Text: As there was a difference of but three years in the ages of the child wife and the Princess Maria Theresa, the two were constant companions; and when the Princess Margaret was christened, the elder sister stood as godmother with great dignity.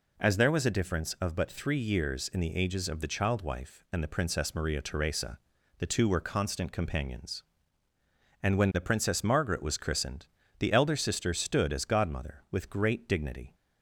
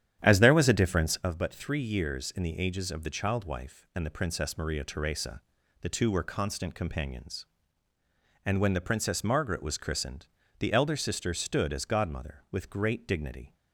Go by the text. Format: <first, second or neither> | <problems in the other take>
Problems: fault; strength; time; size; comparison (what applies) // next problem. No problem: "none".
first | starts louder than the rest; strong; until 1.3 s; 10 dB